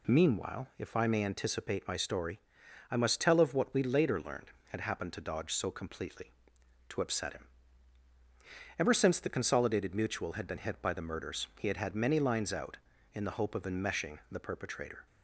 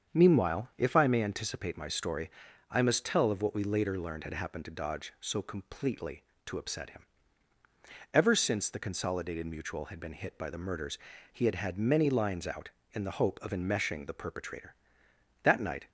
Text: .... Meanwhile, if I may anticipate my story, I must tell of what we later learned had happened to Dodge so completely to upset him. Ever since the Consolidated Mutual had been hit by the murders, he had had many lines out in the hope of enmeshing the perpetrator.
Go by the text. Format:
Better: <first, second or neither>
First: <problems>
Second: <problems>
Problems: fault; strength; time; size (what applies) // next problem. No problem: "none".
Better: first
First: none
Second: starts louder than the rest; strong; until 1.1 s; 7.5 dB // goes on to say "That night"; slight; from 15.4 s on; 0.46 s long